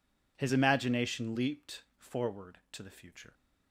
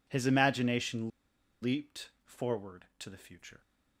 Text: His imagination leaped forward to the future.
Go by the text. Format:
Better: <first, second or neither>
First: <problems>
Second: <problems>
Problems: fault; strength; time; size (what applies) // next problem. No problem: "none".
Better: first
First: none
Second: pauses between "imagination" and "leaped"; noticeable; at 1.0 s; 0.52 s long